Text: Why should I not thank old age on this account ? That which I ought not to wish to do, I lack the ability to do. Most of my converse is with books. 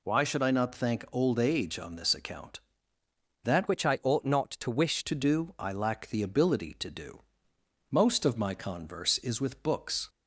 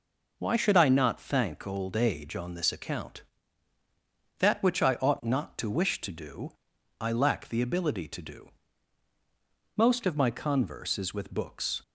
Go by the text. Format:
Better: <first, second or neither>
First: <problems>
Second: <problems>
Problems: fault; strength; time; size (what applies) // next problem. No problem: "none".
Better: second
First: changes voice from "which" to "wish"; from 3.6 to 5.0 s; 1.4 s long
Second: none